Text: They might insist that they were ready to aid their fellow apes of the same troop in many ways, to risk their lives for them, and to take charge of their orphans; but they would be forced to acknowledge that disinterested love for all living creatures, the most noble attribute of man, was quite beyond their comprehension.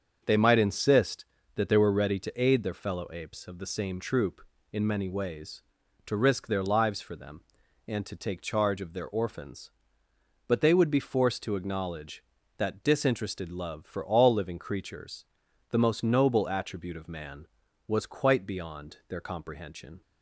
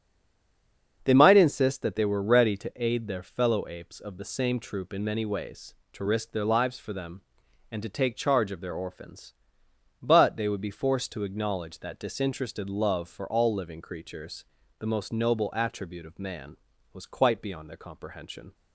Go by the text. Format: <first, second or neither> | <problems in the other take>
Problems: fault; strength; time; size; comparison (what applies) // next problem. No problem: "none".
first | stays silent before the first word; until 1.0 s; 1.0 s long // starts louder than the rest; until 2.0 s; 7 dB; also in the first